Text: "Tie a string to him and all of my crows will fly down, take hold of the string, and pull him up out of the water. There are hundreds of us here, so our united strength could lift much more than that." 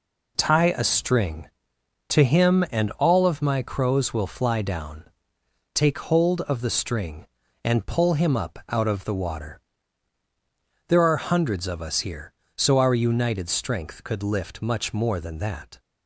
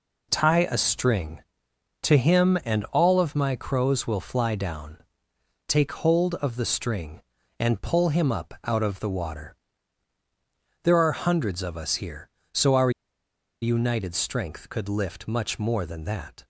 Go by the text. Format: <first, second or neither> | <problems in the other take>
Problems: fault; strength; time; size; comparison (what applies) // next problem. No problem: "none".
first | pauses between "our" and "united"; noticeable; at 12.8 s; 0.72 s long